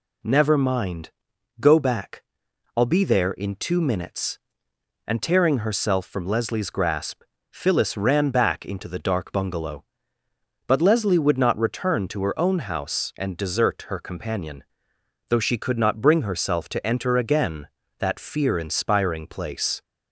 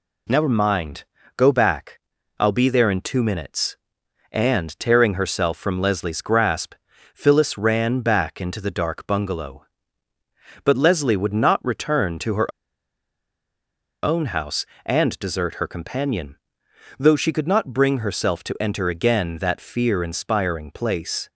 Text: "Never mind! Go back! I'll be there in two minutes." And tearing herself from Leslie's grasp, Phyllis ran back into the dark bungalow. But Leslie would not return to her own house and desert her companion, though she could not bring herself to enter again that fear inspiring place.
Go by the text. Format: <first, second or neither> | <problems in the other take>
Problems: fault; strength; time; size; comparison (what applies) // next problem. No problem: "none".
first | pauses between "her" and "own"; strong; at 12.5 s; 1.5 s long